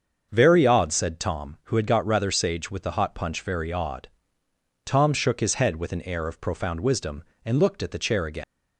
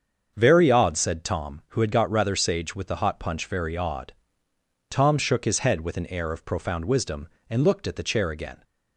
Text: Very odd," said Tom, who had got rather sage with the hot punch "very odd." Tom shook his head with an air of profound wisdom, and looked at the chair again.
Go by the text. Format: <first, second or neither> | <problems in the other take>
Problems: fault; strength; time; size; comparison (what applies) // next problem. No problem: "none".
second | starts louder than the rest; until 1.3 s; 6.5 dB; also in the second // leaves "again" unfinished; at 8.4 s; 150 ms